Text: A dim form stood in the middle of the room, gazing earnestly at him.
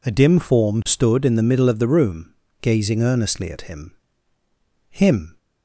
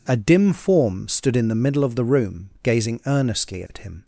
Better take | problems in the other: second | says "him" twice; at 4.8 s

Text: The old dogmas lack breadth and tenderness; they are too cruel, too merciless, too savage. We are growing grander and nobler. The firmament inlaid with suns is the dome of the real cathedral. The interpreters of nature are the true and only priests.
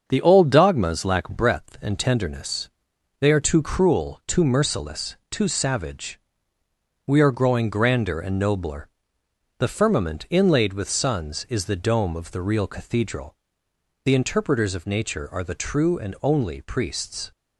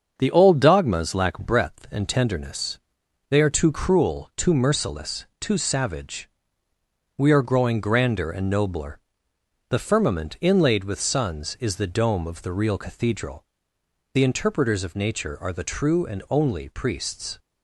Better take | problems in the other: neither | starts louder than the rest; the same in both

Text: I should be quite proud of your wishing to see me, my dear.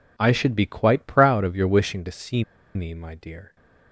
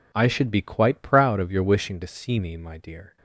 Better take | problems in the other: second | pauses between "see" and "me"; slight; at 2.4 s; 0.32 s long

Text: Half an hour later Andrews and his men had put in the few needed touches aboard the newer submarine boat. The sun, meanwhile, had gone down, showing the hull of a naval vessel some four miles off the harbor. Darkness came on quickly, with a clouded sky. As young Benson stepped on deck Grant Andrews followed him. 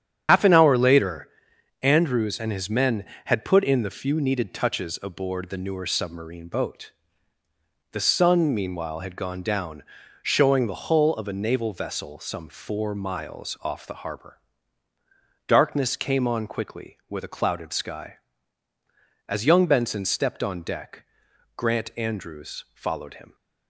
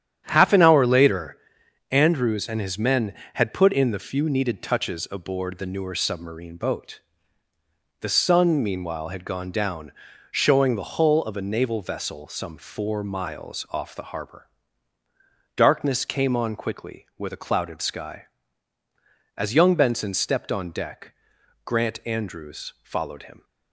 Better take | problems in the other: second | loses the start of "Half"; at 0.2 s; 120 ms // starts louder than the rest; strong; until 1.2 s; 8.5 dB; strong in the second // pauses between "later" and "Andrews"; noticeable; at 1.2 s; 0.54 s long; noticeable in the second // pauses between "deck" and "Grant"; noticeable; at 21.0 s; 0.52 s long; noticeable in the second

